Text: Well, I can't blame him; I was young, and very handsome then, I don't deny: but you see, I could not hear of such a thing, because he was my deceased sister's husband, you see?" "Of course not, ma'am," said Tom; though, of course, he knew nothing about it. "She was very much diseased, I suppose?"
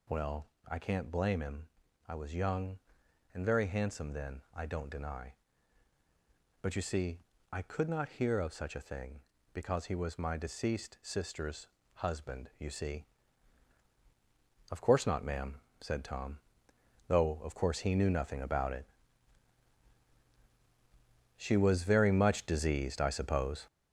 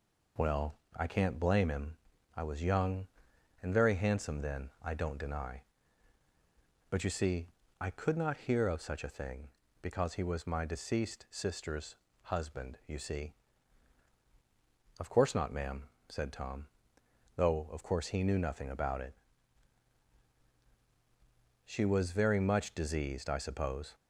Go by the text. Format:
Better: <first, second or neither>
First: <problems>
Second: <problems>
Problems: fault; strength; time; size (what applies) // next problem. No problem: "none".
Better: second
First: gets louder; throughout; 6.5 dB // pauses between "sister's" and "husband"; slight; at 11.6 s; 0.30 s long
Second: pauses between "sister's" and "husband"; slight; at 11.9 s; 0.30 s long